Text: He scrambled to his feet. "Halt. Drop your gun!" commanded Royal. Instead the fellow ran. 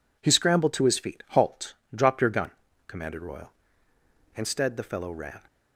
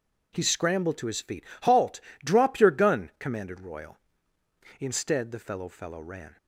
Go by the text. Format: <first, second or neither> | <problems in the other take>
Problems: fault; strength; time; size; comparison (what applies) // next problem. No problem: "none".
first | says "fellow" twice; at 5.6 s